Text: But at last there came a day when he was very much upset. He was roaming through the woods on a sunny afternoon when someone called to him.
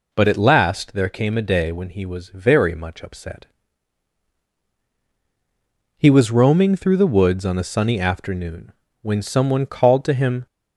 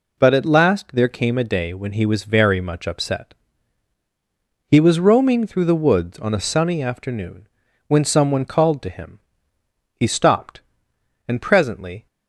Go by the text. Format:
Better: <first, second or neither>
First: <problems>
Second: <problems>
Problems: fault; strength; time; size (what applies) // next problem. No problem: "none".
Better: first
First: pauses between "afternoon" and "when"; slight; at 8.7 s; 0.30 s long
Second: pauses between "afternoon" and "when"; at 7.4 s; 0.40 s long // goes on to say "He stopped And presently"; strong; from 9.9 s on; 2.1 s long